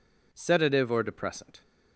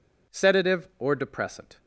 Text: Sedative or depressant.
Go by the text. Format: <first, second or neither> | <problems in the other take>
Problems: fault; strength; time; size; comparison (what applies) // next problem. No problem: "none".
neither | none